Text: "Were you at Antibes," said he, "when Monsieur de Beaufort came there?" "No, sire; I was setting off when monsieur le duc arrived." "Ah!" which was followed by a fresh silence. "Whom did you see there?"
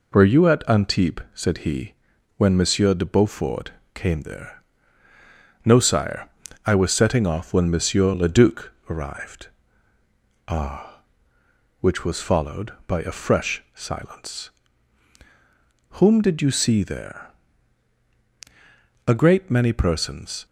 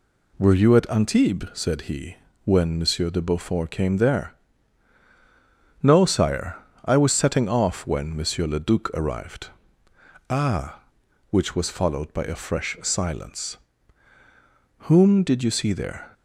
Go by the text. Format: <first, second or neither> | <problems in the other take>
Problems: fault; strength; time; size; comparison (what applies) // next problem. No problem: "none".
second | pauses between "Beaufort" and "came"; slight; at 3.7 s; 0.24 s long // pauses between "duc" and "arrived"; slight; at 8.7 s; 0.20 s long // goes on to say "A great many persons"; from 19.0 s on; 1.3 s long